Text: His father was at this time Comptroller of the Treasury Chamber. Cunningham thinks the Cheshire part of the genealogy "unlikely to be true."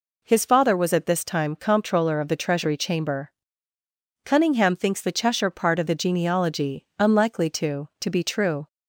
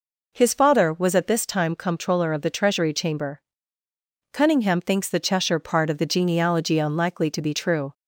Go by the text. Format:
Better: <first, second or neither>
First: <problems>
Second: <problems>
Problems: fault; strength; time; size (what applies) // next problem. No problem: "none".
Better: second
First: says "to" twice; at 7.9 s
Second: none